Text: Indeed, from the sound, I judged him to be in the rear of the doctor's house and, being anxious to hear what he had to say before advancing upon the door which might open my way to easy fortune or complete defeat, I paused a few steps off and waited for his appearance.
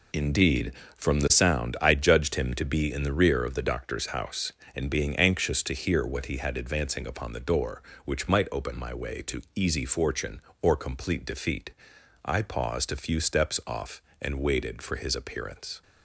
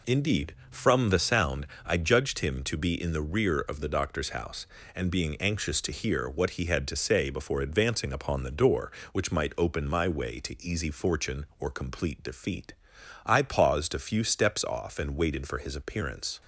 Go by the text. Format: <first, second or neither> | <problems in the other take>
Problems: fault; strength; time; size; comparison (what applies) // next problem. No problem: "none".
second | skips "to say before"; at 6.5 s